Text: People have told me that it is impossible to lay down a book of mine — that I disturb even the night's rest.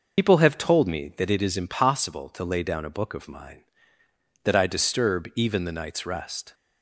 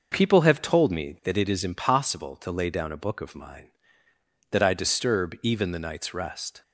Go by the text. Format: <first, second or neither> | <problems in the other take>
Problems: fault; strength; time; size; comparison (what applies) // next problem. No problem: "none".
second | loses the start of "People"; at 0.1 s; 100 ms